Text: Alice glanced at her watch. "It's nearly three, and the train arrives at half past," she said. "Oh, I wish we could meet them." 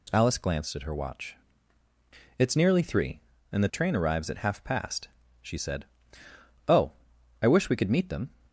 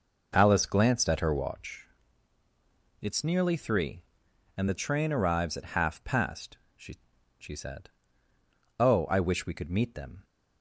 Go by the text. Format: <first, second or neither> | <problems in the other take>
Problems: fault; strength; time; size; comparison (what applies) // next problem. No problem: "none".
first | says "she" twice; at 7.3 s